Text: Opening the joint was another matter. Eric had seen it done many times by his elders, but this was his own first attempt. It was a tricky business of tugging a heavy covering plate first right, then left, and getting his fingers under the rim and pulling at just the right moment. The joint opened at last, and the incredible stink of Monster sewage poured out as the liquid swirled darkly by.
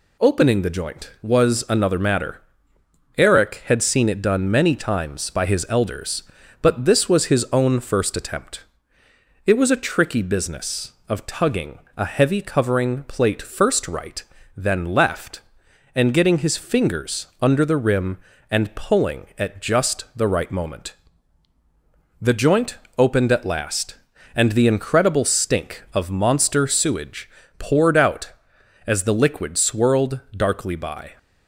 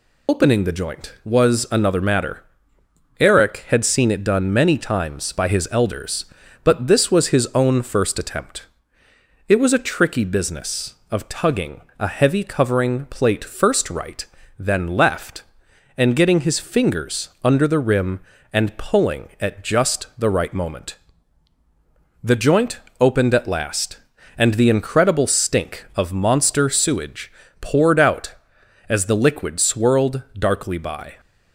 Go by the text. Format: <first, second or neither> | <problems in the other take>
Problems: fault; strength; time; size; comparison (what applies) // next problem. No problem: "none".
first | loses the start of "Opening"; at 0.2 s; 70 ms // pauses between "tugging" and "a"; slight; at 11.7 s; 0.18 s long; slight in the first // pauses between "joint" and "opened"; slight; at 22.7 s; 0.20 s long; slight in the first // pauses between "sewage" and "poured"; slight; at 27.3 s; 0.30 s long; slight in the first